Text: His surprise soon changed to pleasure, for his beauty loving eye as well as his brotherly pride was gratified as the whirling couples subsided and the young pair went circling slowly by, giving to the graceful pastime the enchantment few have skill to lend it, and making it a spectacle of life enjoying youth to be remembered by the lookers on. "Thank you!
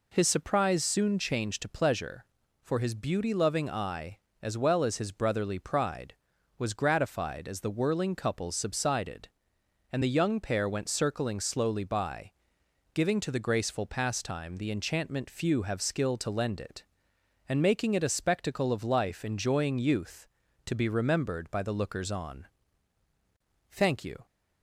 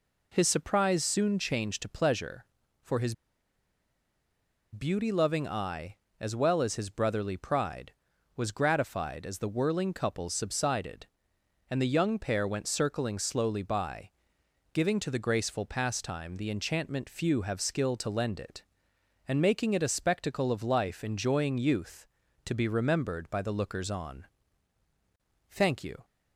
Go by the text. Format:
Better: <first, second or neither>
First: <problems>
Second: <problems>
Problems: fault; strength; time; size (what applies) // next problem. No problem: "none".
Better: first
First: none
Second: pauses between "his" and "beauty"; strong; at 3.1 s; 1.6 s long